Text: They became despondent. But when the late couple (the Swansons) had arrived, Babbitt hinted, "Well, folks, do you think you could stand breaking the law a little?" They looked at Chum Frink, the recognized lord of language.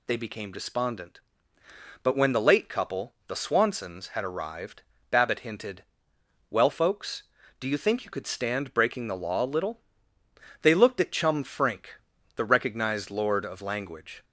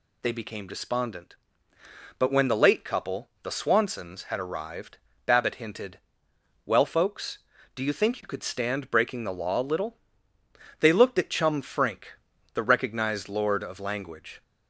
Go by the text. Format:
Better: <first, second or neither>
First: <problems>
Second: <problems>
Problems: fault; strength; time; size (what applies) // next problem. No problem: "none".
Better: neither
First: none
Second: none